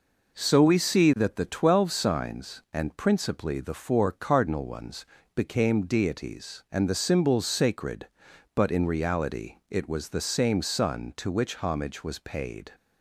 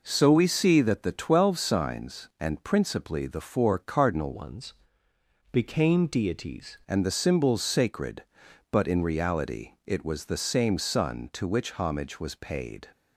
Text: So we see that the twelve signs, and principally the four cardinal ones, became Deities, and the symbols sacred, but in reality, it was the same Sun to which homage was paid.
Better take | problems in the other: first | changes voice from "ones" to "Deities"; from 4.3 to 6.7 s; 2.4 s long

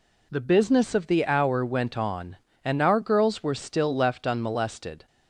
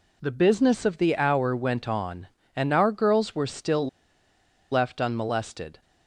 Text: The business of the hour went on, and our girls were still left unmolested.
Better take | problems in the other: first | pauses between "still" and "left"; noticeable; at 3.8 s; 0.83 s long

